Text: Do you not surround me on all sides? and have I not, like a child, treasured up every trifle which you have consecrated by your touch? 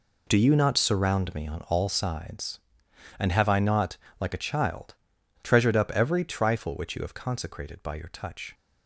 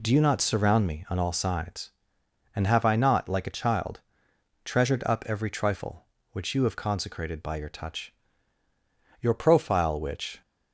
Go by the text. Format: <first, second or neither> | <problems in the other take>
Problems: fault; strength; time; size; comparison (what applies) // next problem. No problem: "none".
first | goes on to say "Your profile which"; noticeable; from 9.2 s on; 1.2 s long